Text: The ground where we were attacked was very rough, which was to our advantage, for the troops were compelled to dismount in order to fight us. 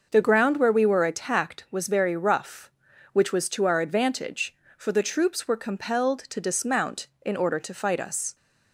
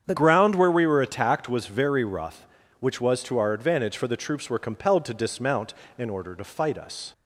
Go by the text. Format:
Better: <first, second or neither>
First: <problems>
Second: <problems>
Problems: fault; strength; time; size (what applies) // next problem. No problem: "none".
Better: first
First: none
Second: starts louder than the rest; strong; until 1.0 s; 8 dB // changes voice at "ground"; from 0.1 s on; 7.0 s long